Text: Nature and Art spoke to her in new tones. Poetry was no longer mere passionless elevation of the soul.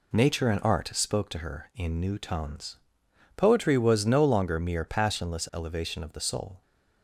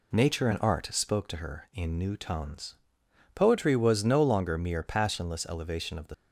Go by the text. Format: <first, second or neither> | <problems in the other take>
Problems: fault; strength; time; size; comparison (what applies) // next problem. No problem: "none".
first | stops before "soul"; at 6.1 s